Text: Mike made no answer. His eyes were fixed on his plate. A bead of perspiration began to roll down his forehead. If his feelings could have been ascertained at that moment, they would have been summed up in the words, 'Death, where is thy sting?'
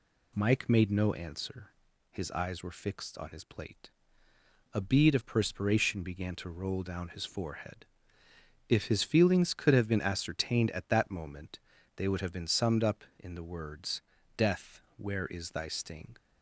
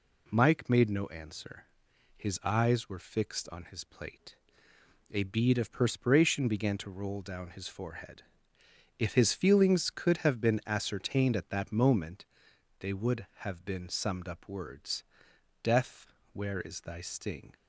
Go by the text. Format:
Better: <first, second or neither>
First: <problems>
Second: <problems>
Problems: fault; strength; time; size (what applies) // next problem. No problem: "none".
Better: first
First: none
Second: skips "in the"; at 14.4 s